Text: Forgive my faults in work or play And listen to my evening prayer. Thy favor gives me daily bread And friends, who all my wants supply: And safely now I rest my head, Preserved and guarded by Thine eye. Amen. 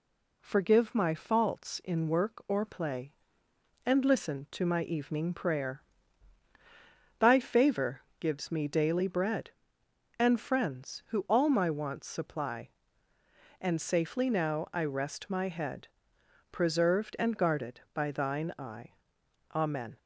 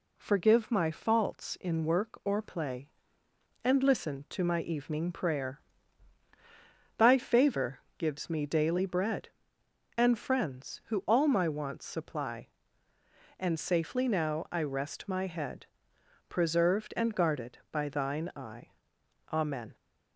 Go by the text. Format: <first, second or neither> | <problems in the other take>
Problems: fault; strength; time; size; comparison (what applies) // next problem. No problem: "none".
neither | pauses between "favor" and "gives"; slight; the same in both